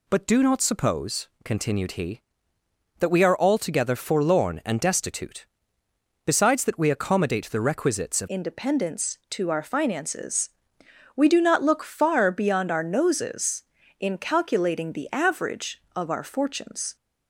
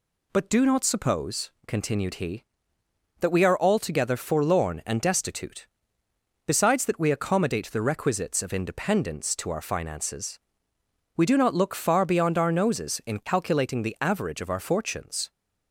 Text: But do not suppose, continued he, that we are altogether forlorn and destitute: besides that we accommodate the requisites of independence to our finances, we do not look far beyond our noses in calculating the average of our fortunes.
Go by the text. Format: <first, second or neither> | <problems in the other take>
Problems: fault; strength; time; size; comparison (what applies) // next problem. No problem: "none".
second | changes voice at "independence"; from 8.2 s on; 8.7 s long